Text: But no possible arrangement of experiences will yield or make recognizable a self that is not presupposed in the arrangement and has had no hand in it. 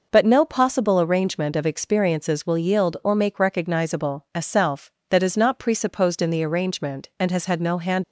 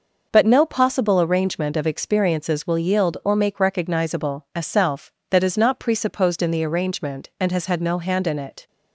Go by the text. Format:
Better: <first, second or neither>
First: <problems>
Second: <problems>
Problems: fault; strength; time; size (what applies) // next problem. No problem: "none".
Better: second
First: stops before "in it"; at 8.0 s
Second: none